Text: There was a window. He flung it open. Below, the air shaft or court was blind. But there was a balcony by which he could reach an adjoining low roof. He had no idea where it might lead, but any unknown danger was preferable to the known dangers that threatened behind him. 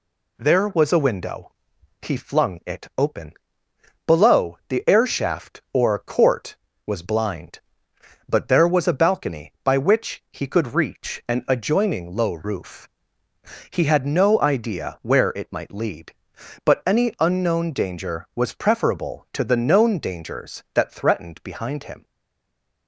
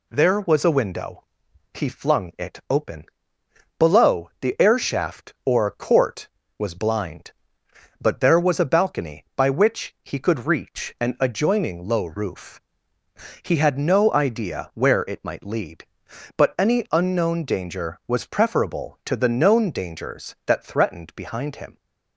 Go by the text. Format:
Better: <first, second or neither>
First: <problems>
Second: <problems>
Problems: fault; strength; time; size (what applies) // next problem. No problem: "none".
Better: second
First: stays silent after the last word; slight; from 22.0 s on; 0.8 s long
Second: none